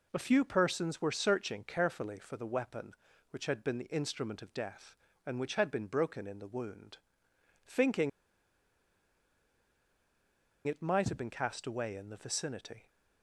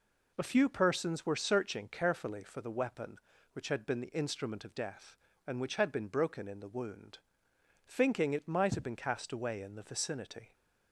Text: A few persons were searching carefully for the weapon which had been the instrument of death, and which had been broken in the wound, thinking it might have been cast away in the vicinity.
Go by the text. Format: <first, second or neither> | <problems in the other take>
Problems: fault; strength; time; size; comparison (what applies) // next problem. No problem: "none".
second | pauses between "thinking" and "it"; strong; at 8.0 s; 2.5 s long